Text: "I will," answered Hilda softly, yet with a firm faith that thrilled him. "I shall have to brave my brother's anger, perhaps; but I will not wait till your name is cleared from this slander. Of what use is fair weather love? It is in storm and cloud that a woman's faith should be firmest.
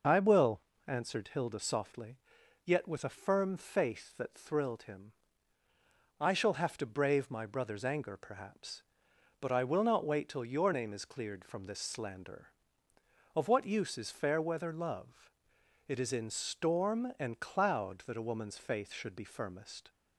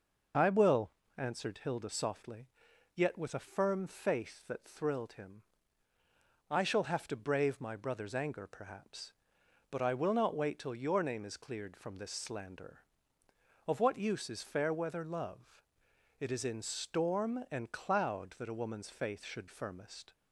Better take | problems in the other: first | skips "be"; at 19.4 s

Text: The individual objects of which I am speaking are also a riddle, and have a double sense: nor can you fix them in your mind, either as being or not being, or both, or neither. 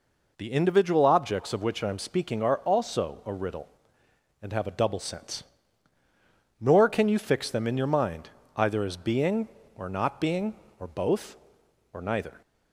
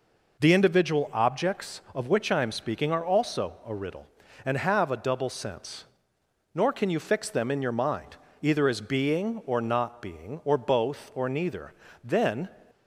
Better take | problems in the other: first | goes on to say "Then"; slight; from 12.0 s on; 0.46 s long

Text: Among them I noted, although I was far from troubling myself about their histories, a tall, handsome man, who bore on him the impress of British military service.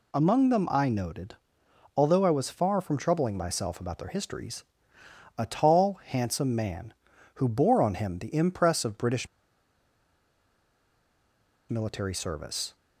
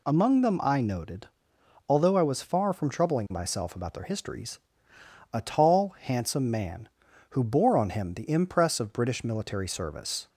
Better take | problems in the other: second | pauses between "British" and "military"; strong; at 9.2 s; 2.4 s long

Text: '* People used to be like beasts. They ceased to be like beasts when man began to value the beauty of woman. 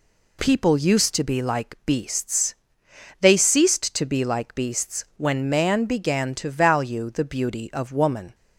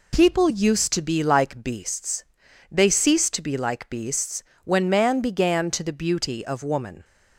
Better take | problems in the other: first | pauses between "beasts" and "when"; slight; at 4.4 s; 0.20 s long // skips "value"; at 5.8 s

